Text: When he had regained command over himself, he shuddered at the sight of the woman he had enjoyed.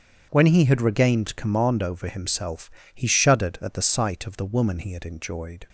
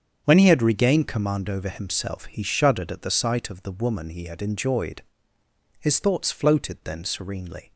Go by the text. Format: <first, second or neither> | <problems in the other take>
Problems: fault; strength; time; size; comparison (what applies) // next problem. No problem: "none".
first | starts louder than the rest; strong; until 1.2 s; 7.5 dB; strong in the first // goes on to say "His thoughts floated then serenely"; strong; from 5.7 s on; 1.9 s long